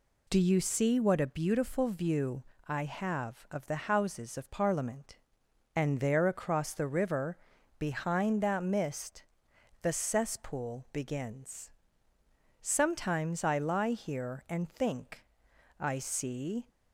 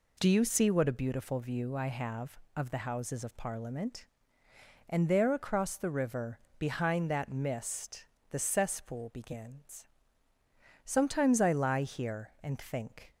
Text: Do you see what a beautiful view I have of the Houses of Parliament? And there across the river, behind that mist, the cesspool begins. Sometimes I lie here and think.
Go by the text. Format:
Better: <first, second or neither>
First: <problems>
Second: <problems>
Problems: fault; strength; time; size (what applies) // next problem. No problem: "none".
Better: second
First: pauses between "view" and "I"; slight; at 2.4 s; 0.26 s long // goes on to say "I see"; noticeable; from 15.8 s on; 0.88 s long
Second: none